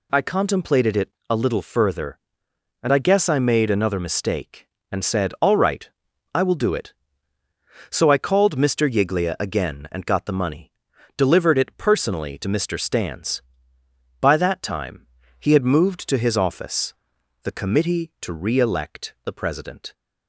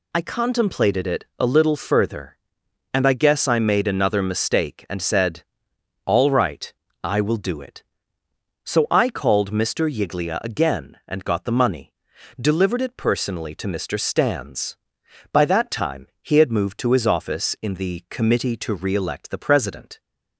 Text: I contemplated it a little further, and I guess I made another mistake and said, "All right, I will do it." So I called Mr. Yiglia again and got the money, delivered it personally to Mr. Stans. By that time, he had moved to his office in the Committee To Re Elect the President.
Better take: second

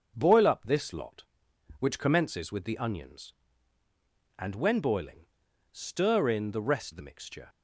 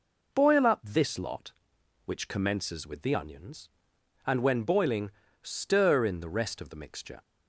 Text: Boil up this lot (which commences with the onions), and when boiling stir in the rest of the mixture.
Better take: second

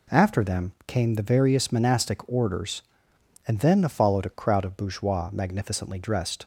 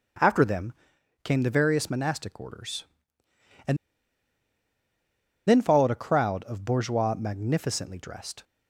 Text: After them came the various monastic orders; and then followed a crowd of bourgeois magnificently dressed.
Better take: first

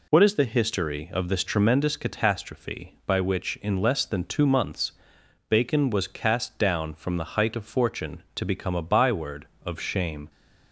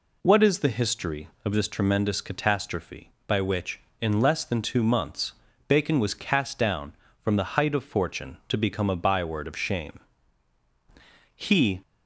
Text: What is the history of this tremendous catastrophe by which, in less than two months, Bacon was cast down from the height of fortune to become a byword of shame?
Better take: first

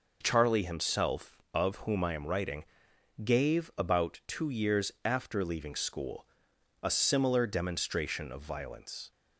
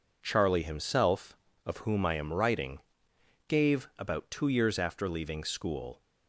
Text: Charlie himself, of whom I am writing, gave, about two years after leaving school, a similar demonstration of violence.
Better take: first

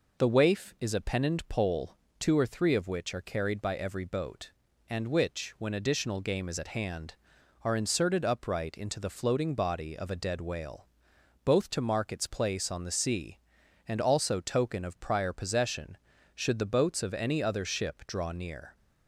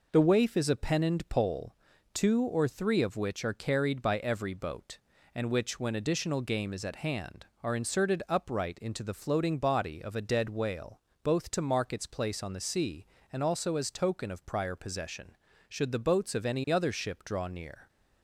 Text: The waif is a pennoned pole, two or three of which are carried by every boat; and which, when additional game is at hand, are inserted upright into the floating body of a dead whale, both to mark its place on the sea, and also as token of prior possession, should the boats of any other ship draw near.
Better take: second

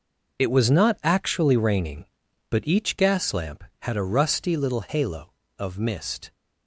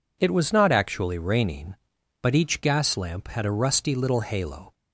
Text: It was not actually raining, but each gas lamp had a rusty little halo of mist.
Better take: first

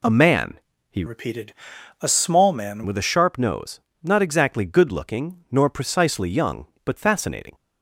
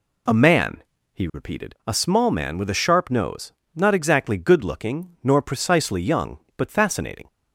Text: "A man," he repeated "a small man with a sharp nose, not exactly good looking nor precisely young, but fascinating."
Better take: second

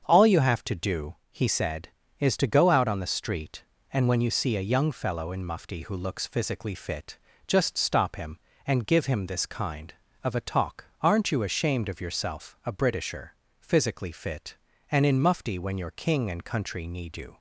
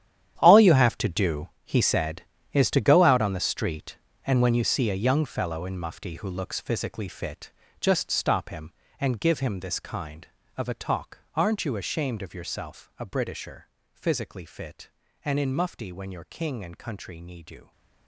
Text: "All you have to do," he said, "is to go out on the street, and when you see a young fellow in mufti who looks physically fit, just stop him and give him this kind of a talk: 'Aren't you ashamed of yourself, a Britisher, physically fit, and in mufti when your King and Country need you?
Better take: first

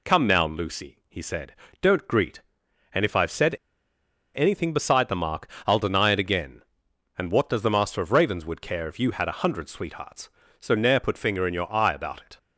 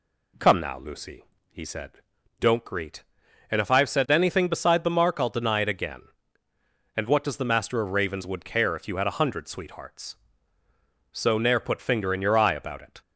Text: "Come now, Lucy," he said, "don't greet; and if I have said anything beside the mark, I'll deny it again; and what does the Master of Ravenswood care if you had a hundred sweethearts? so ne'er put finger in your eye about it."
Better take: second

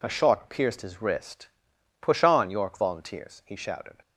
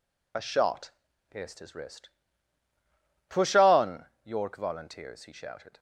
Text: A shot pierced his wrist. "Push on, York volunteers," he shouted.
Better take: first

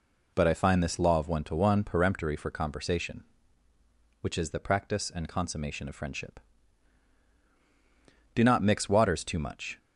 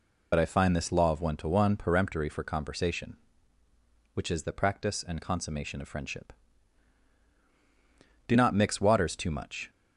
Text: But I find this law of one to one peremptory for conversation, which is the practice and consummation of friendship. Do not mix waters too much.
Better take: first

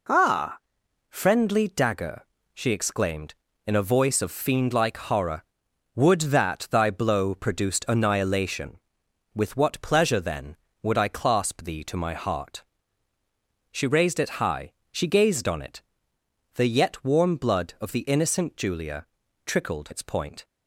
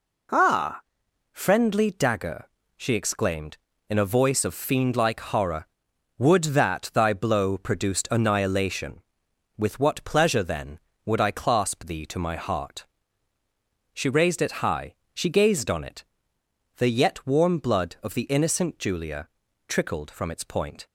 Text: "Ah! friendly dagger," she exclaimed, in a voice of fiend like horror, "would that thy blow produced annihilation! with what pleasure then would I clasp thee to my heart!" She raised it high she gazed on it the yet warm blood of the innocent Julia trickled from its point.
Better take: second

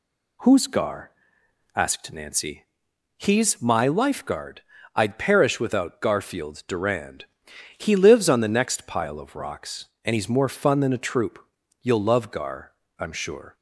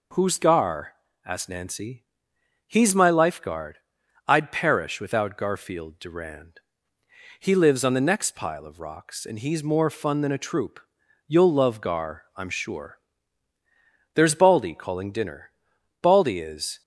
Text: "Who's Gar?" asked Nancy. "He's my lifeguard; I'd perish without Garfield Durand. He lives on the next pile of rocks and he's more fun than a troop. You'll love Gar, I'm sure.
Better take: first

